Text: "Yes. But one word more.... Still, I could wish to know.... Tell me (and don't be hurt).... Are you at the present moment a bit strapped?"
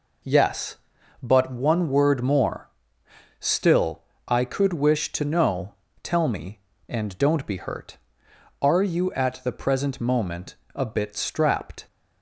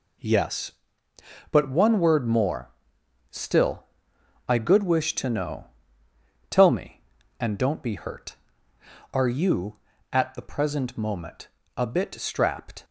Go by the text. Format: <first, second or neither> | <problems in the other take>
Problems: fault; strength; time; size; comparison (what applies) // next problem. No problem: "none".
first | says "good" for "could"; at 4.5 s // pauses between "moment" and "a"; slight; at 11.4 s; 0.30 s long; slight in the first